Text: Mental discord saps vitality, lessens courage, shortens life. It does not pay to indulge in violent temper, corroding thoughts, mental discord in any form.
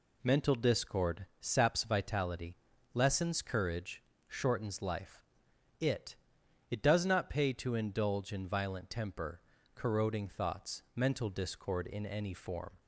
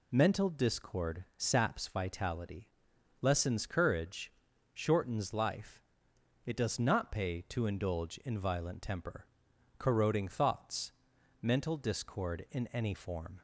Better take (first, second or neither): second